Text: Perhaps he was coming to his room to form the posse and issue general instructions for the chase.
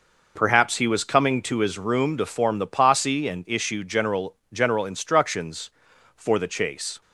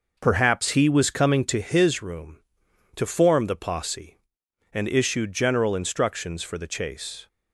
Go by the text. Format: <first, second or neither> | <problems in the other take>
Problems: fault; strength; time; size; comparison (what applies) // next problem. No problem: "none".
second | says "general" twice; at 4.5 s